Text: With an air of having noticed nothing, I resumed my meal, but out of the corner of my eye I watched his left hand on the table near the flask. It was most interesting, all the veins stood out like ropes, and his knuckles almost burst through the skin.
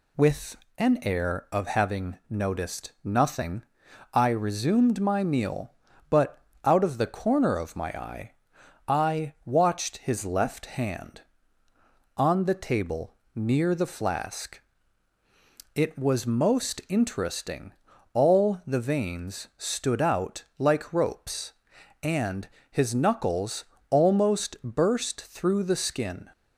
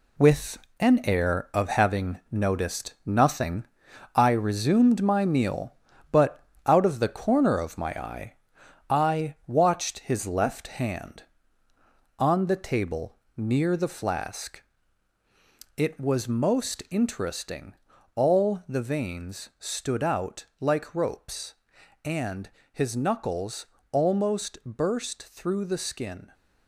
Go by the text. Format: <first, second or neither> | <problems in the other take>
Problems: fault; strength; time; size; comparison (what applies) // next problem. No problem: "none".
first | gets quieter; strong; throughout; 8 dB // pauses between "With" and "an"; slight; at 0.5 s; 0.22 s long; slight in the first // pauses between "but" and "out"; slight; at 6.4 s; 0.24 s long; slight in the first // pauses between "eye" and "I"; noticeable; at 8.3 s; 0.56 s long; noticeable in the first // pauses between "table" and "near"; slight; at 13.1 s; 0.20 s long; slight in the first // pauses between "and" and "his"; slight; at 22.4 s; 0.22 s long; slight in the first // pauses between "knuckles" and "almost"; slight; at 23.6 s; 0.24 s long; slight in the first